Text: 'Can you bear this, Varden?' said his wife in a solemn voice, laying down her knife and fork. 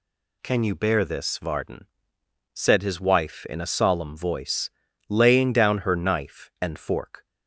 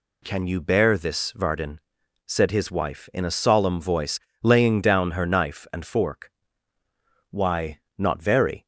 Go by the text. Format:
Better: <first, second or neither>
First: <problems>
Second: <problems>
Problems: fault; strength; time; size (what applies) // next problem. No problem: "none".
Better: first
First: none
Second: goes on to say "Why not very"; from 7.2 s on; 1.3 s long